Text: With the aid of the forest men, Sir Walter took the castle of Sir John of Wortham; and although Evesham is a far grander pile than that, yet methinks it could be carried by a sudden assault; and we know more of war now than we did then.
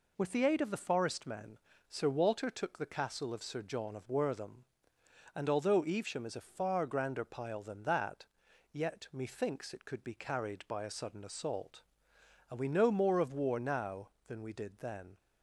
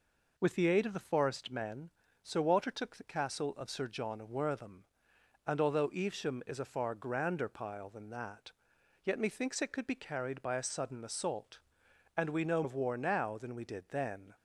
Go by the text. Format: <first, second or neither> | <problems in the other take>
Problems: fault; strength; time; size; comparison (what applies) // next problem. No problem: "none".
first | skips "more"; at 12.6 s